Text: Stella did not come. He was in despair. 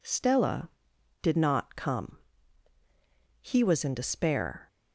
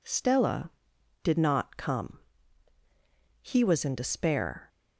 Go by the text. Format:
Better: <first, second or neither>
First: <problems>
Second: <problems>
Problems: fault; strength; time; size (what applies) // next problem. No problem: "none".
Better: neither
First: none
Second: none